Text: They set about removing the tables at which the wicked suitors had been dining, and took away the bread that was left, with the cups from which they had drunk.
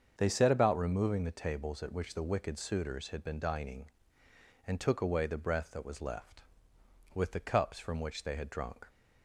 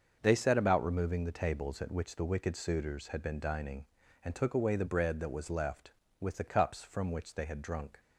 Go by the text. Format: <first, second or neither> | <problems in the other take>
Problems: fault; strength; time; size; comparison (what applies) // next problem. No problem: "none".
second | starts louder than the rest; until 1.1 s; 7 dB; also in the second // says "breath" for "bread"; at 5.3 s